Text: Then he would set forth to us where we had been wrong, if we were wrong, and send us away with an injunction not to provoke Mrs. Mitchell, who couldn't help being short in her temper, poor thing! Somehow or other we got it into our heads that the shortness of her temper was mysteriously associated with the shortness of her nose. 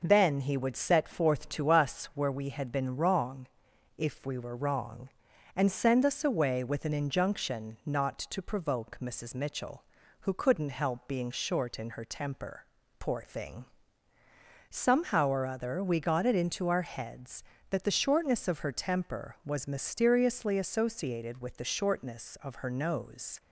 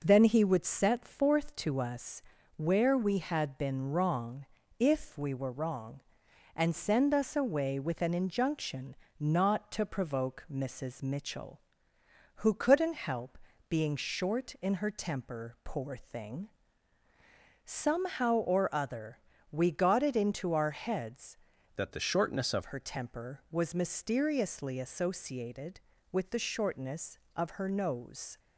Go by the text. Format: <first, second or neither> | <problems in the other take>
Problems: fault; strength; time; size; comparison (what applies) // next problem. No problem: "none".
first | pauses between "us" and "where"; slight; at 2.2 s; 0.36 s long // pauses between "injunction" and "not"; slight; at 8.9 s; 0.24 s long // pauses between "help" and "being"; slight; at 13.3 s; 0.32 s long // pauses between "other" and "we"; slight; at 19.1 s; 0.32 s long // changes voice from "that" to "of"; from 21.7 to 22.6 s; 0.9 s long